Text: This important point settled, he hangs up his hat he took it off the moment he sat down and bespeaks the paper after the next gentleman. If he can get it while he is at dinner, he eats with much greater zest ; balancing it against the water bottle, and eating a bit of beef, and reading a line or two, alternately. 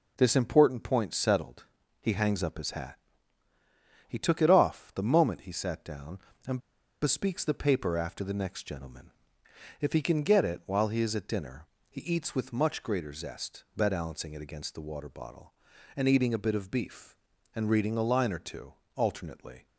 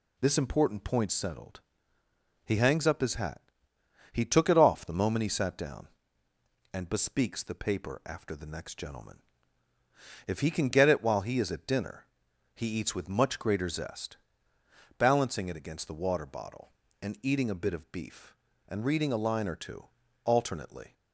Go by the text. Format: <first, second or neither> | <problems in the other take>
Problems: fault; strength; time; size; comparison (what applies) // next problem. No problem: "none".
second | pauses between "hat" and "he"; at 2.9 s; 1.1 s long; noticeable in the second // pauses between "and" and "bespeaks"; at 6.5 s; 0.42 s long